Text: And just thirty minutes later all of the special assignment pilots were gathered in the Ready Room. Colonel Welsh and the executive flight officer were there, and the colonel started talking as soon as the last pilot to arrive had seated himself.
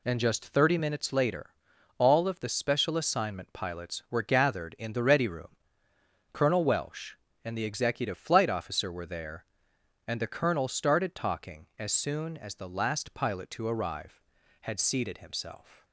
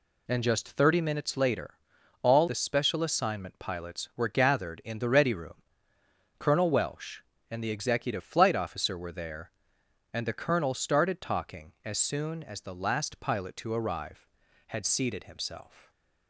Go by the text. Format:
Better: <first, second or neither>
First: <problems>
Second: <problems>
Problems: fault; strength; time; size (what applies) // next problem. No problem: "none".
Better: first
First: pauses between "later" and "all"; noticeable; at 1.4 s; 0.48 s long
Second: pauses between "later" and "all"; noticeable; at 1.7 s; 0.48 s long // skips "of"; at 2.4 s // stays silent after the last word; slight; from 15.7 s on; 0.5 s long